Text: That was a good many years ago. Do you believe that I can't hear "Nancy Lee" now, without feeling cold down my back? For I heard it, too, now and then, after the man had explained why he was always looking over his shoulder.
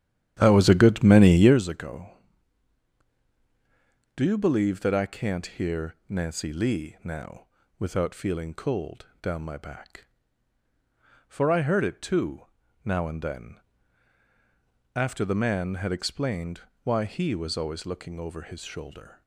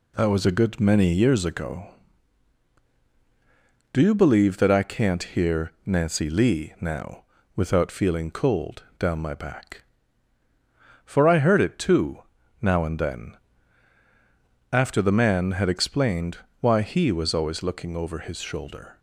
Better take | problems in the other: second | starts louder than the rest; strong; until 1.6 s; 10.5 dB // pauses between "cold" and "down"; slight; at 9.0 s; 0.16 s long; slight in the second // pauses between "explained" and "why"; slight; at 16.6 s; 0.22 s long; slight in the second

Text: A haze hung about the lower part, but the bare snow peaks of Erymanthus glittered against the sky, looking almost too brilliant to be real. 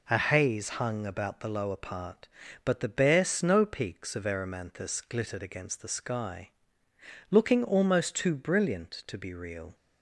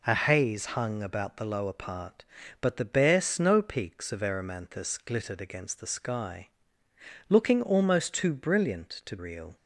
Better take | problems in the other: first | skips "be"; at 9.1 s

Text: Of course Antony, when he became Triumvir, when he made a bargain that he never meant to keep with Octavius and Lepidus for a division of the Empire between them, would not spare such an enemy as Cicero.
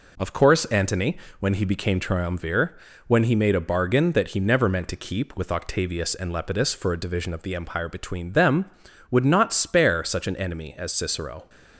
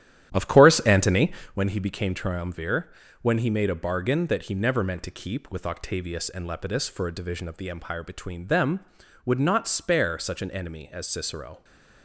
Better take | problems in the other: first | starts louder than the rest; strong; until 1.7 s; 11.5 dB

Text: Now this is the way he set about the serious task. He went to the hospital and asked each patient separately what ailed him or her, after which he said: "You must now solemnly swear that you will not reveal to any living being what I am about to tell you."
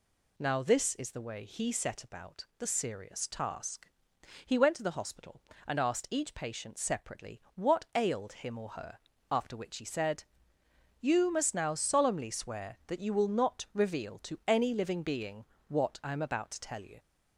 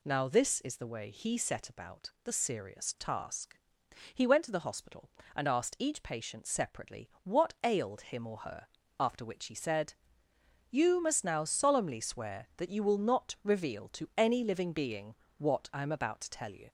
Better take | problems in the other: neither | pauses between "being" and "what"; slight; the same in both

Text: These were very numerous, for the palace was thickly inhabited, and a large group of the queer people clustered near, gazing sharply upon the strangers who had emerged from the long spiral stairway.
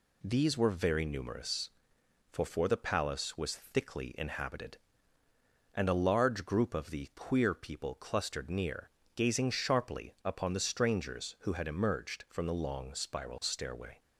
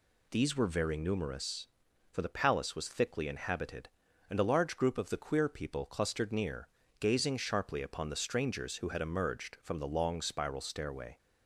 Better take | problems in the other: second | says "for" twice; at 2.4 s

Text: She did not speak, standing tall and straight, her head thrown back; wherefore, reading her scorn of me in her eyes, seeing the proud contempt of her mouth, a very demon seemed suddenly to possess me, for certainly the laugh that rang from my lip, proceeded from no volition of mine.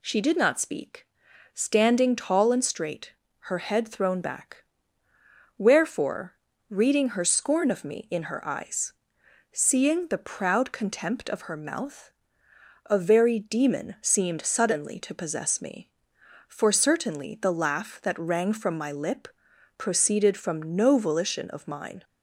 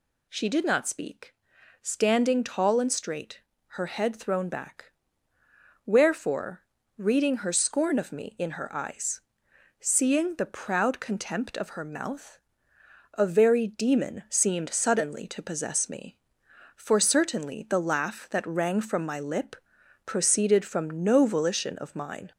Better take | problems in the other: first | gets louder; slight; throughout; 2.5 dB

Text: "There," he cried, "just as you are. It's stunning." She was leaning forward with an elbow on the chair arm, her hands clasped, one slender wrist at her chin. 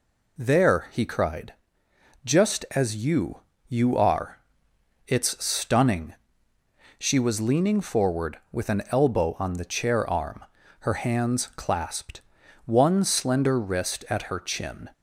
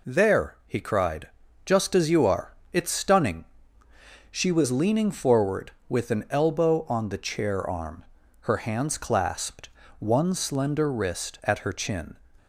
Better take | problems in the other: second | says "you" twice; at 3.6 s

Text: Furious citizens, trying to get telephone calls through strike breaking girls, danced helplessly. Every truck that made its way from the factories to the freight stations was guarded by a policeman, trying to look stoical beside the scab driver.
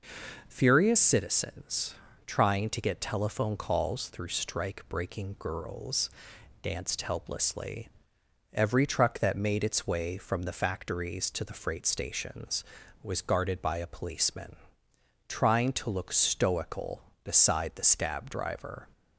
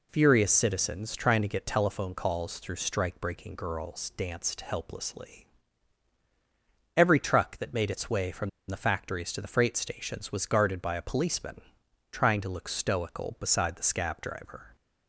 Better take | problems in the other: first | pauses between "from" and "the"; slight; at 8.4 s; 0.19 s long

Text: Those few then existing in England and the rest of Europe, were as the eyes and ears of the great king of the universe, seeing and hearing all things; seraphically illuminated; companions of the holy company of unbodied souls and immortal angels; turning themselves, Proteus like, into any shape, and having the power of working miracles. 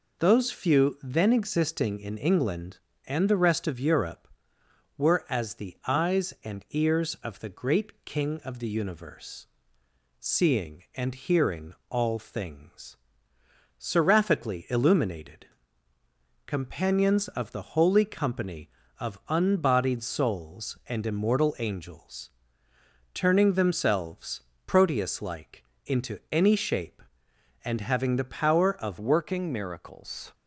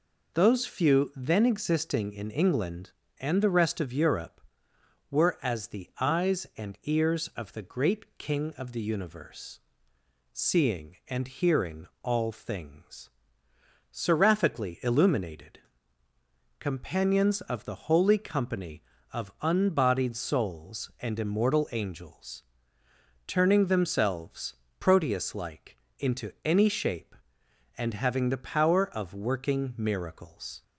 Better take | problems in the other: second | pauses between "hearing" and "all"; slight; at 11.7 s; 0.16 s long; slight in the second // changes voice at "working"; from 28.9 s on; 1.4 s long

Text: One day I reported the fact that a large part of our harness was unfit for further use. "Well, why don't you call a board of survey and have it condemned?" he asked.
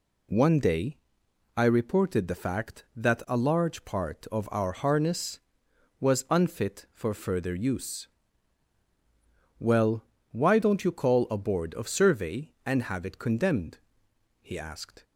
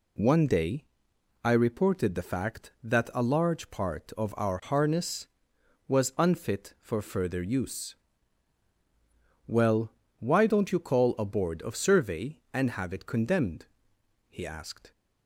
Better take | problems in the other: neither | pauses between "day" and "I"; noticeable; the same in both

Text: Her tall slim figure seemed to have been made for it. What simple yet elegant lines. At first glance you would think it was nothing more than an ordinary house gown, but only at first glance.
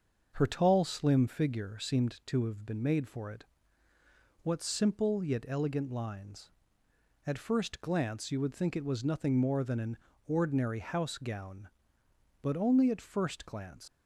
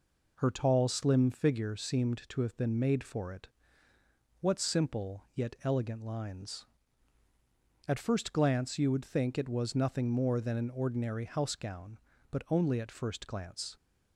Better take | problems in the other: second | starts louder than the rest; until 1.3 s; 6.5 dB // pauses between "an" and "ordinary"; slight; at 9.9 s; 0.30 s long // leaves "glance" unfinished; at 13.8 s; 115 ms

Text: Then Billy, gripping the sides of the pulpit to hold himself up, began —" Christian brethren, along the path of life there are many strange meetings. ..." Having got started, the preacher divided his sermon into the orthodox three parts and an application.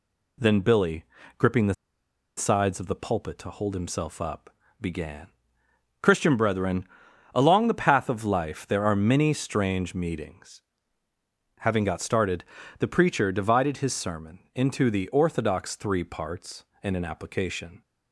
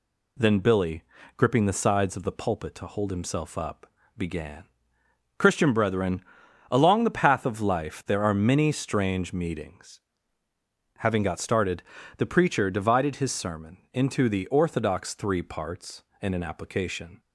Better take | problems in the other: second | pauses between "the" and "sides"; noticeable; at 1.7 s; 0.64 s long

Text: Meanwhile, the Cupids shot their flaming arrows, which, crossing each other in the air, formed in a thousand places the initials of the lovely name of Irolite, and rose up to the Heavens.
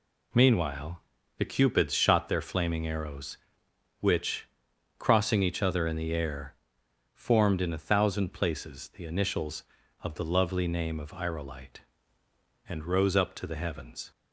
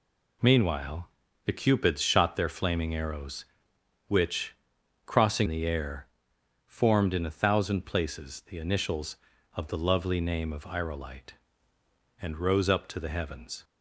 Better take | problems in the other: first | skips "each other in"; at 5.4 s

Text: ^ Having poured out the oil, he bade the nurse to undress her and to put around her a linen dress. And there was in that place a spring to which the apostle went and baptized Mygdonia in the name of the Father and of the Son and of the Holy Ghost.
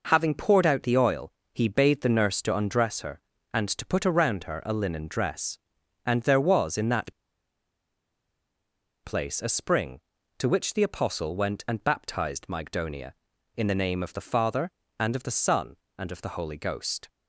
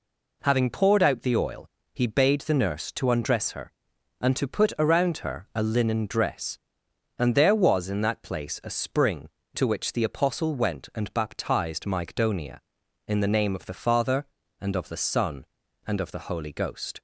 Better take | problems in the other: second | pauses between "that" and "place"; strong; at 7.1 s; 1.9 s long

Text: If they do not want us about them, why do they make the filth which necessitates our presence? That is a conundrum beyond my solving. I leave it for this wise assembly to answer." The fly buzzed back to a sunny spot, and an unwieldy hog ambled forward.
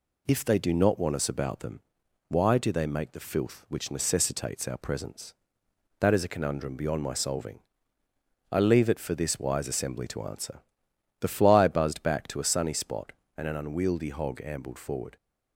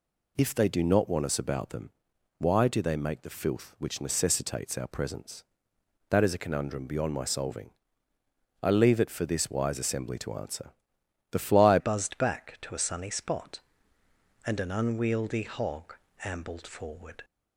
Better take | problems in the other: first | changes voice at "buzzed"; from 11.7 s on; 5.5 s long // pauses between "hog" and "ambled"; slight; at 15.9 s; 0.30 s long

